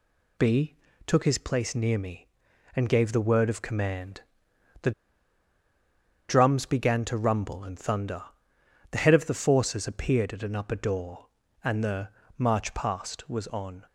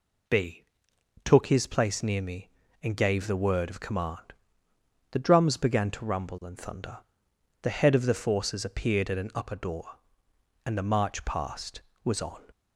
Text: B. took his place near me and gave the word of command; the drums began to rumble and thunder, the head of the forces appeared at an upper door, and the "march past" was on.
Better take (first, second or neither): second